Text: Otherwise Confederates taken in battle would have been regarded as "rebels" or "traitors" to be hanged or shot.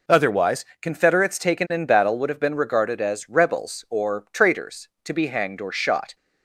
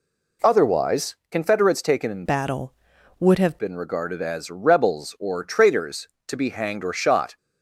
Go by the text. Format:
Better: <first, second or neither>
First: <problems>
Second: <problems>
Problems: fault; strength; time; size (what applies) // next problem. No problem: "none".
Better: first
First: pauses between "Otherwise" and "Confederates"; slight; at 0.6 s; 0.18 s long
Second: pauses between "Otherwise" and "Confederates"; slight; at 1.1 s; 0.16 s long // changes voice from "battle" to "have"; from 2.2 to 3.5 s; 1.3 s long